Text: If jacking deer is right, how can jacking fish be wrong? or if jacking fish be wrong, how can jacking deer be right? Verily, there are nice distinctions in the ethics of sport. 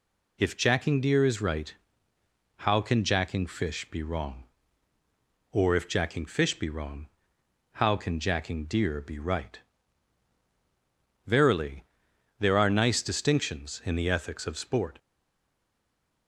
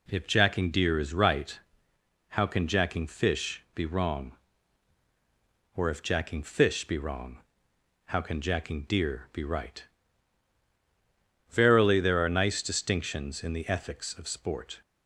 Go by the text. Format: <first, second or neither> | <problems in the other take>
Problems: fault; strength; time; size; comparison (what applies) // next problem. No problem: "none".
second | stays silent after the last word; noticeable; from 14.9 s on; 1.3 s long